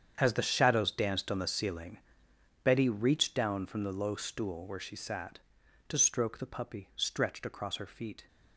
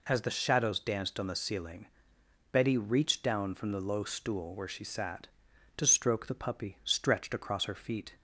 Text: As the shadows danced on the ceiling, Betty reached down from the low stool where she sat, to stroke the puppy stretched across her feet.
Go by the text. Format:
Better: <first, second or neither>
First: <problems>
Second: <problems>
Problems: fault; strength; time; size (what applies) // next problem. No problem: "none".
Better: second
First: gets quieter; strong; throughout; 14.5 dB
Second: none